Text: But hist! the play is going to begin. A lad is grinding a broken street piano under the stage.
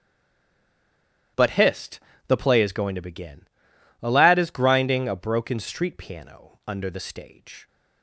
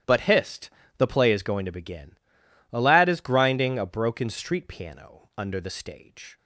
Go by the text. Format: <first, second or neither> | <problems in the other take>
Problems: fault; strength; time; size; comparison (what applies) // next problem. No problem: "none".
second | stays silent before the first word; noticeable; until 1.3 s; 1.3 s long // starts louder than the rest; strong; until 2.6 s; 12 dB; strong in the second